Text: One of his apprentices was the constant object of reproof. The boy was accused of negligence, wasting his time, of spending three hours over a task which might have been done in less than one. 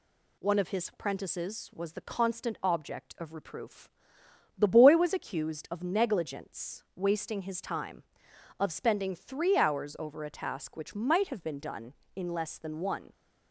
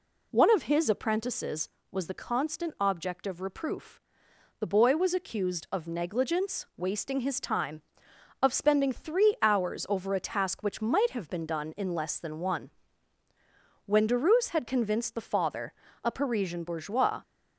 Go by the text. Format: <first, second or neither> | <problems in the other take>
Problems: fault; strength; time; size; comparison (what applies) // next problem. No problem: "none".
first | goes on to say "When Derues had convinced the father a Parisian bourgeois"; strong; from 13.8 s on; 3.3 s long